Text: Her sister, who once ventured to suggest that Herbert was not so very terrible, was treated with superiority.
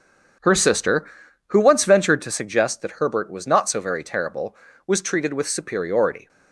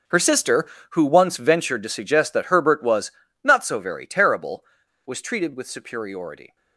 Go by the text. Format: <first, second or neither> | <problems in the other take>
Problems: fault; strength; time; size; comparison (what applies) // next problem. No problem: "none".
first | gets quieter; strong; throughout; 16.5 dB // starts louder than the rest; until 1.3 s; 6.5 dB; also in the first // pauses between "was" and "not"; slight; at 3.1 s; 0.32 s long